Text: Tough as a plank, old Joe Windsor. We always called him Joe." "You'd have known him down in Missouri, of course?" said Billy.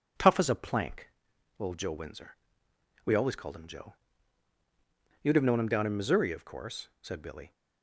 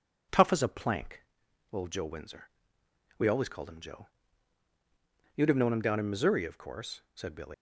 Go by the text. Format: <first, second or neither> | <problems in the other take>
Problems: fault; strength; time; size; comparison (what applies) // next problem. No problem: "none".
first | leaves "Billy" unfinished; at 7.5 s; 105 ms